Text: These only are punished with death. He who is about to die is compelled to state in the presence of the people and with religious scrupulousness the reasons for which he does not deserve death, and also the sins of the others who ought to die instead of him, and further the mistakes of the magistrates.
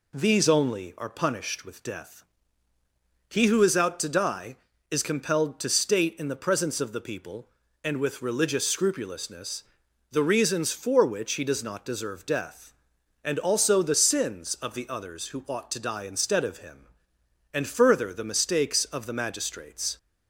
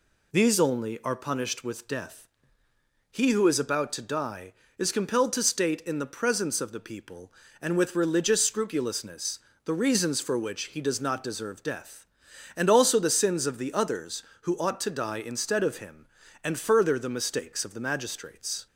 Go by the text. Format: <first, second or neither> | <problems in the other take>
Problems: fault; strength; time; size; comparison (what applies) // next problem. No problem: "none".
second | says "out" for "about"; at 3.7 s // pauses between "scrupulousness" and "the"; noticeable; at 9.6 s; 0.48 s long; slight in the second